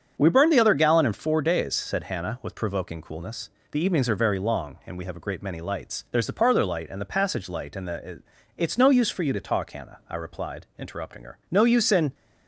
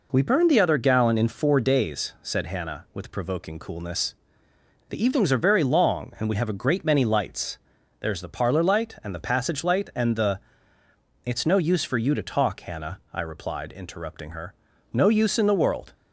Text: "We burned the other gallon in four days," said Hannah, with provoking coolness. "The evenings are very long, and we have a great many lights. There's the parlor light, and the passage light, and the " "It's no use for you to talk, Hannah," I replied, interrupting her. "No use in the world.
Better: second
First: starts louder than the rest; strong; until 1.1 s; 8 dB // stops before "the world"; at 12.1 s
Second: none

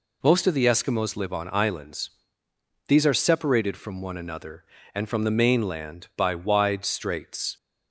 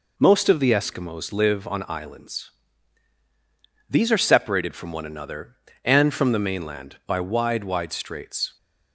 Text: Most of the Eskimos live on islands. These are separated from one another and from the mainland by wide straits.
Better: first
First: none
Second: says "wide" twice; at 7.6 s

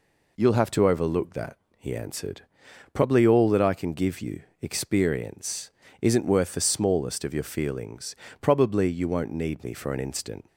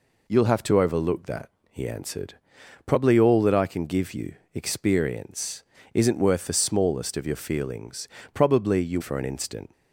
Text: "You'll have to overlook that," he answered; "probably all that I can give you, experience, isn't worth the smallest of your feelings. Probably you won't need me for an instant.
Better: first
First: none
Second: skips "won't need me"; at 8.9 s

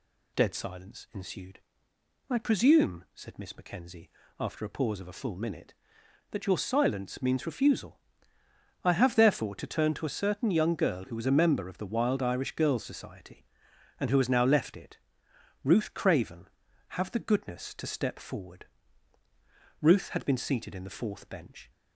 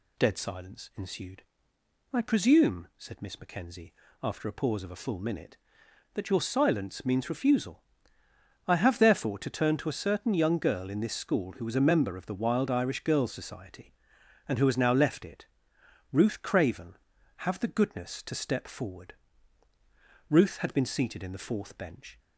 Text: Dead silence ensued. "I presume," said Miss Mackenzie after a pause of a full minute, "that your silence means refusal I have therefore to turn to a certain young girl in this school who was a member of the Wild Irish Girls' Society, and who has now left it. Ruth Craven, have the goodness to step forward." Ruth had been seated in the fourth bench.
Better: second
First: pauses between "Mackenzie" and "after"; slight; at 4.0 s; 0.32 s long // pauses between "refusal" and "I"; noticeable; at 7.9 s; 0.84 s long // skips "in this school"; at 11.0 s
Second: pauses between "Mackenzie" and "after"; slight; at 3.9 s; 0.32 s long // pauses between "refusal" and "I"; noticeable; at 7.8 s; 0.84 s long

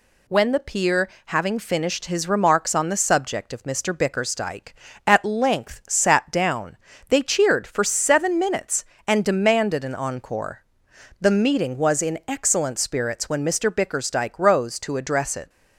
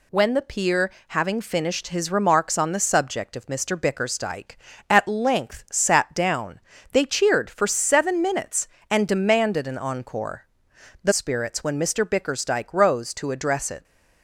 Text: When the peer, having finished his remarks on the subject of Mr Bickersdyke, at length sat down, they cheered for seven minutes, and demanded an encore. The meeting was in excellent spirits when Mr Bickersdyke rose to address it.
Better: first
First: none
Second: skips "meeting was in excellent"; at 11.1 s

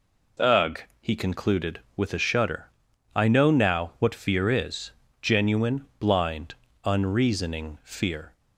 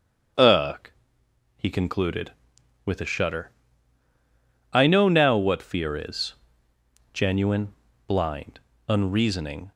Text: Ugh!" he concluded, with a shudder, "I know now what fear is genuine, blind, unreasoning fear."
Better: first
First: pauses between "is" and "genuine"; slight; at 4.9 s; 0.28 s long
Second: starts louder than the rest; strong; until 2.0 s; 7.5 dB // pauses between "is" and "genuine"; noticeable; at 6.3 s; 0.80 s long // stops before "fear"; at 9.7 s

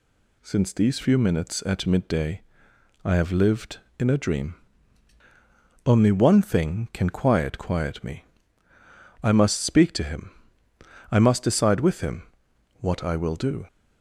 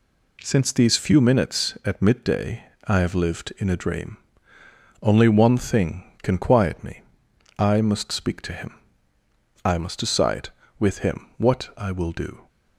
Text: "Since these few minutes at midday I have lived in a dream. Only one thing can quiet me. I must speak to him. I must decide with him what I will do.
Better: second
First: pauses between "midday" and "I"; noticeable; at 2.4 s; 0.62 s long // says "quiet" twice; at 7.5 s // pauses between "him" and "what"; noticeable; at 12.2 s; 0.58 s long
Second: pauses between "midday" and "I"; slight; at 2.6 s; 0.24 s long

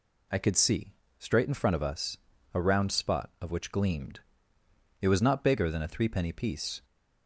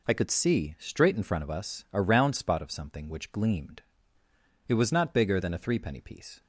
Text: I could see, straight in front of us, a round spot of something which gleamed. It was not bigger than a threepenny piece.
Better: second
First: skips "something"; at 3.5 s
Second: none

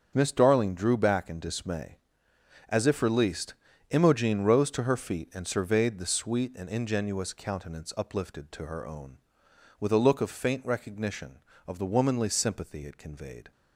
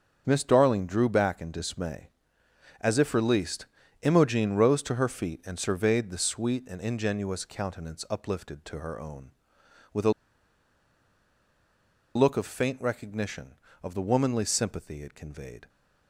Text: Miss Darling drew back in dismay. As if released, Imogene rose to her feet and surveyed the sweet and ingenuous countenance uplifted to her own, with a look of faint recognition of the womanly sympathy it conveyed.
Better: first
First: starts louder than the rest; until 1.1 s; 7 dB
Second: starts louder than the rest; until 1.2 s; 7 dB // pauses between "a" and "look"; strong; at 10.1 s; 2.0 s long

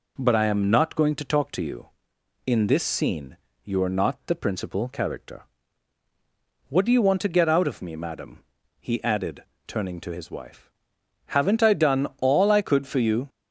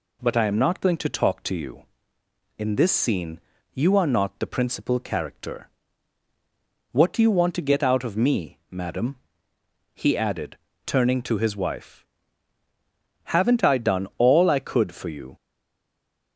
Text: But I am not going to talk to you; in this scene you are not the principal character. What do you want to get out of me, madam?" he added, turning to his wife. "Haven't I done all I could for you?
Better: first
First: pauses between "scene" and "you"; slight; at 3.3 s; 0.28 s long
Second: pauses between "scene" and "you"; slight; at 3.3 s; 0.34 s long // stays silent after the last word; from 15.3 s on; 1.0 s long

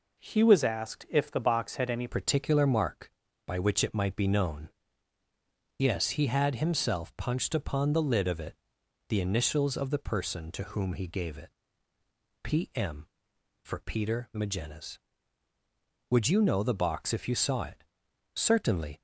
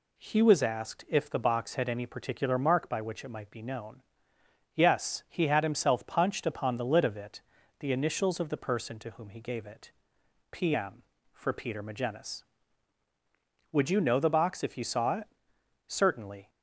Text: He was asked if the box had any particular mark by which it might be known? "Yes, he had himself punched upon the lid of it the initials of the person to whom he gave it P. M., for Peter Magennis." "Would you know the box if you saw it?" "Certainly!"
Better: second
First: changes voice at "particular"; from 2.0 s on; 17.0 s long // pauses between "it" and "the"; noticeable; at 8.5 s; 0.54 s long // pauses between "it" and "P"; noticeable; at 11.4 s; 0.94 s long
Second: pauses between "it" and "the"; at 7.4 s; 0.40 s long // pauses between "it" and "P"; noticeable; at 9.9 s; 0.58 s long

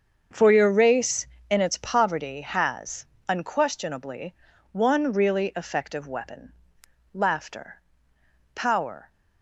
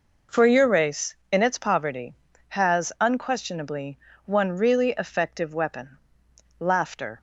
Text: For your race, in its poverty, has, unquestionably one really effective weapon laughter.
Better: second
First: starts louder than the rest; until 1.5 s; 7 dB // pauses between "unquestionably" and "one"; at 4.3 s; 0.38 s long // pauses between "weapon" and "laughter"; noticeable; at 6.5 s; 0.58 s long // goes on to say "Power"; from 8.5 s on; 0.56 s long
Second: pauses between "unquestionably" and "one"; slight; at 3.9 s; 0.28 s long // pauses between "weapon" and "laughter"; noticeable; at 5.9 s; 0.62 s long

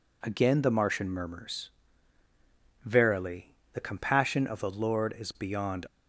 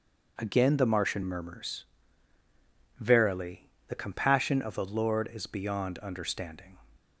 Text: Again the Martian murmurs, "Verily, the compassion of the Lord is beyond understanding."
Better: second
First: stops before "understanding"; at 5.8 s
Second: none

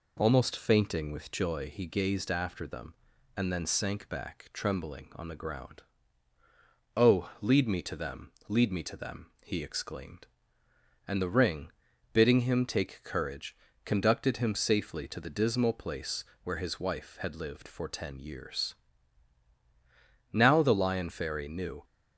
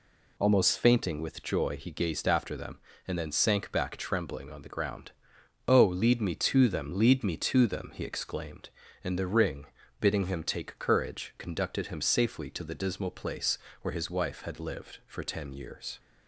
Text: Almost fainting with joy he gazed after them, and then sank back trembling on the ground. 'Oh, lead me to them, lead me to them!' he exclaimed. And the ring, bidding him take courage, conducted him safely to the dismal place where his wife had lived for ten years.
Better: second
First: pauses between "place" and "where"; slight; at 16.2 s; 0.18 s long // goes on to say "Now the Lion Fairy knew"; from 20.3 s on; 1.5 s long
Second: pauses between "place" and "where"; slight; at 13.5 s; 0.24 s long

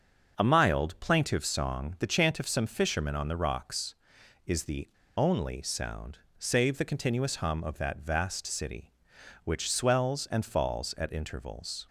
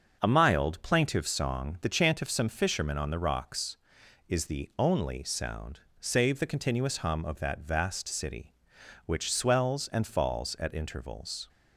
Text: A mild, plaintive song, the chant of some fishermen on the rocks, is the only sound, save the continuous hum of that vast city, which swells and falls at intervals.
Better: second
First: starts louder than the rest; until 1.3 s; 6.5 dB // pauses between "the" and "only"; slight; at 4.8 s; 0.28 s long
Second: starts louder than the rest; until 1.2 s; 6.5 dB

